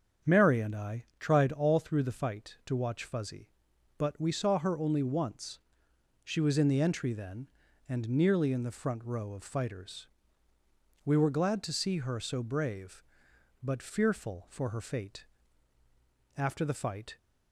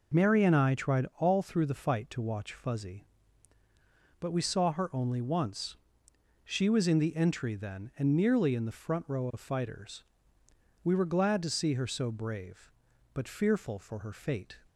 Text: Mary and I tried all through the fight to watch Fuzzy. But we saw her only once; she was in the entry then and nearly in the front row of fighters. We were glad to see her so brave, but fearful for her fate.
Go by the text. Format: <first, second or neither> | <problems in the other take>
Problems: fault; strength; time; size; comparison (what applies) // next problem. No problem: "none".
second | starts louder than the rest; strong; until 1.3 s; 7.5 dB // goes on to say "After the fight"; noticeable; from 16.3 s on; 0.80 s long